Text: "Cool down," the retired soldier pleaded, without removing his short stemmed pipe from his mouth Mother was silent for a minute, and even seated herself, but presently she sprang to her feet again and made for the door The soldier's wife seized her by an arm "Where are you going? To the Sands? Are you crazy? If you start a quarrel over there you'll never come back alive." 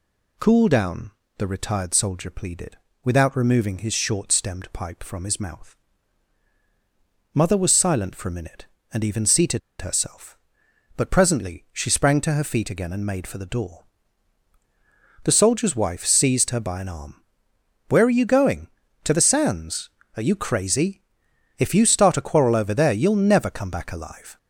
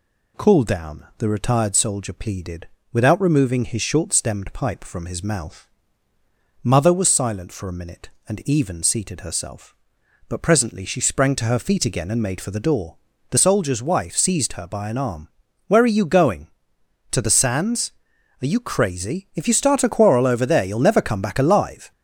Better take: second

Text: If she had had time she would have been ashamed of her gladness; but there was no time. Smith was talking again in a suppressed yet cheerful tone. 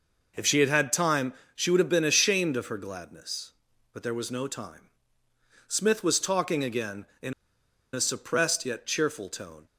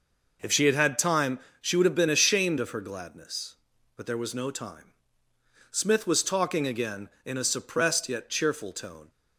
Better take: second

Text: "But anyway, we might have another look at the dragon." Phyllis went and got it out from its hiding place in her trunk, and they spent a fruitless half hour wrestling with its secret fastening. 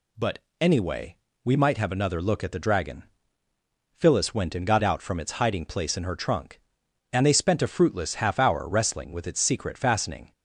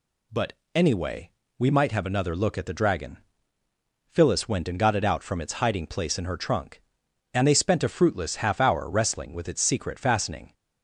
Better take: second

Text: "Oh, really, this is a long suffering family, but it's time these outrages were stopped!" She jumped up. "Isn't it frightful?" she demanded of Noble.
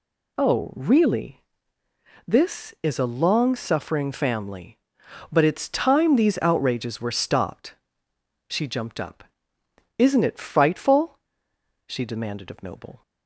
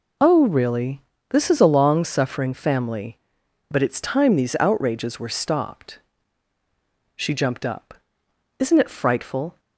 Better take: first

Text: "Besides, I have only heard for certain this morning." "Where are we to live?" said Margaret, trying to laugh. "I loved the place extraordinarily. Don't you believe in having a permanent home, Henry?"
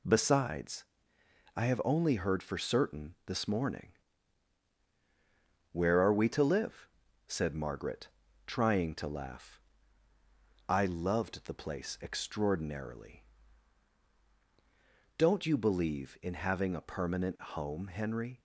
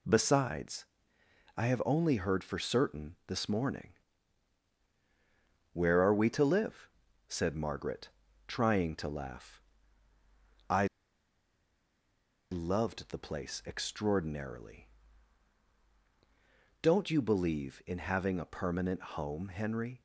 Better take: first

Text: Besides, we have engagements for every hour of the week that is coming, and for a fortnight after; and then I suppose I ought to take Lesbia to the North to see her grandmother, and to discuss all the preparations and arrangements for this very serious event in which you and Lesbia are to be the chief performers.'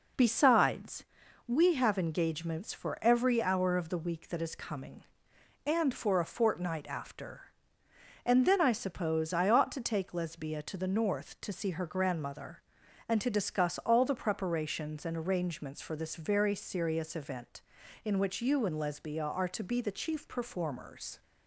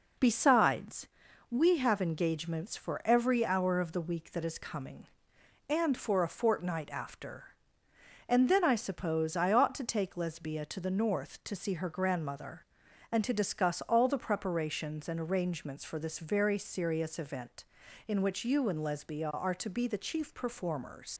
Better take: first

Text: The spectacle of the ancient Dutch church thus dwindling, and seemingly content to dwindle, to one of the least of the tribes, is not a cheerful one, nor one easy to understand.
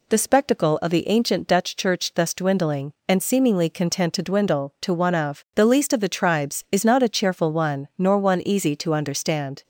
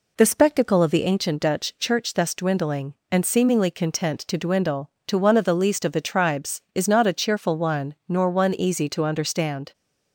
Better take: neither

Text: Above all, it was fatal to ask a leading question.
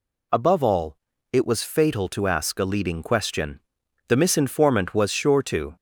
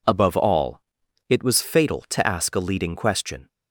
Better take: second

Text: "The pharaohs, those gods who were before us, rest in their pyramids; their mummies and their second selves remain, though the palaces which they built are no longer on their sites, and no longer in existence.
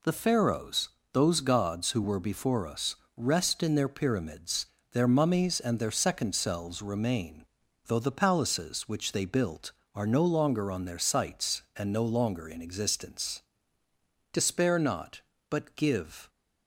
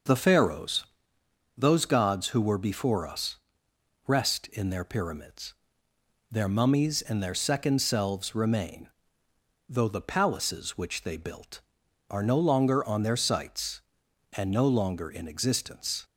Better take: second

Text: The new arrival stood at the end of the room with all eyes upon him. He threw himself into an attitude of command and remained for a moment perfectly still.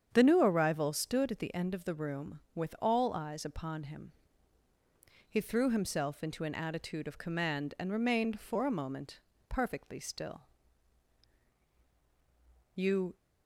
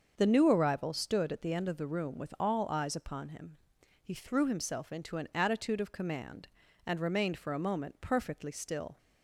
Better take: second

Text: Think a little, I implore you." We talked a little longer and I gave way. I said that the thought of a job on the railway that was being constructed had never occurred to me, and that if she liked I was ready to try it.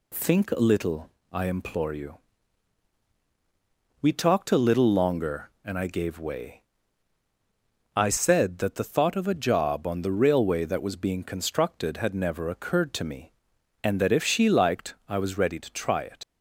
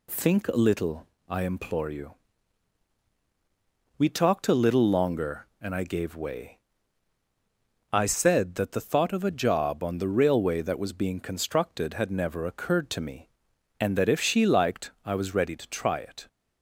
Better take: second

